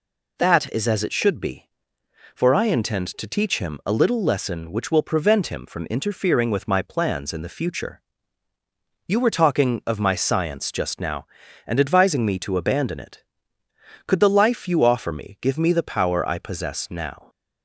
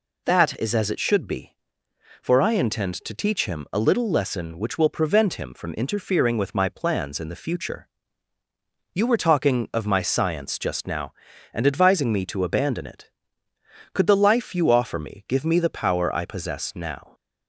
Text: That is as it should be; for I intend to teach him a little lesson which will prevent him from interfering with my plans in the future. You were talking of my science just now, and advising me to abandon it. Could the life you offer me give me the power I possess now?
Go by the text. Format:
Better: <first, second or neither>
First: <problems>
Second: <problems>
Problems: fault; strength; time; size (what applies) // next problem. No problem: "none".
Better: neither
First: none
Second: none